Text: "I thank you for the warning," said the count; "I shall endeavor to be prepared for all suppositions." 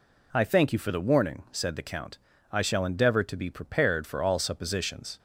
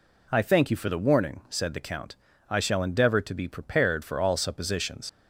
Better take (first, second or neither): first